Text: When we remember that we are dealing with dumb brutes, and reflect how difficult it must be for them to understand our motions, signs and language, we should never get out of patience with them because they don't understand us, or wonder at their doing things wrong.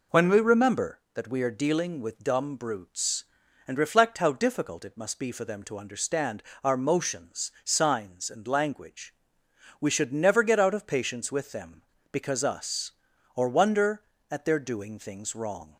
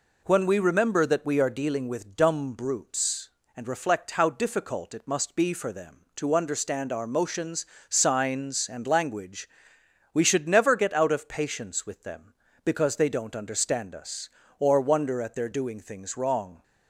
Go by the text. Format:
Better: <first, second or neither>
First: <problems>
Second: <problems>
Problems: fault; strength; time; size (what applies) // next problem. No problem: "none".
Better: second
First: pauses between "understand" and "our"; slight; at 6.4 s; 0.22 s long // skips "they don't understand"; at 12.4 s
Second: none